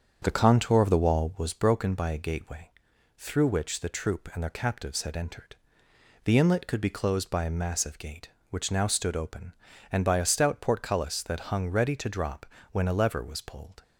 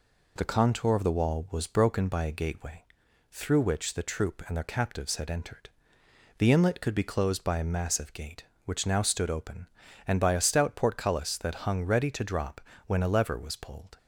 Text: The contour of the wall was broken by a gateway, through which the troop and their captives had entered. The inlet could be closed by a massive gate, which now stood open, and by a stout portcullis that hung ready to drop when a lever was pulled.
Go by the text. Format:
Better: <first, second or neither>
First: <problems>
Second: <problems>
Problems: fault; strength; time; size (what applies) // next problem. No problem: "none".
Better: second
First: starts louder than the rest; strong; until 1.5 s; 7 dB // pauses between "drop" and "when"; slight; at 12.4 s; 0.26 s long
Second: pauses between "drop" and "when"; slight; at 12.5 s; 0.26 s long